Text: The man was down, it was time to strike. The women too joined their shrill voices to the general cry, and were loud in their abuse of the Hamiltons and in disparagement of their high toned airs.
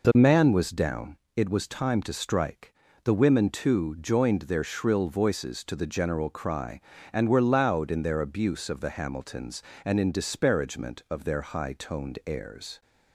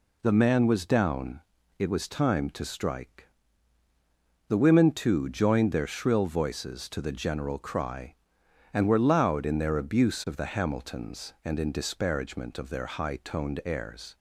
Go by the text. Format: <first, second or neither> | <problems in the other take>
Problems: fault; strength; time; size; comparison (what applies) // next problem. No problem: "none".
neither | none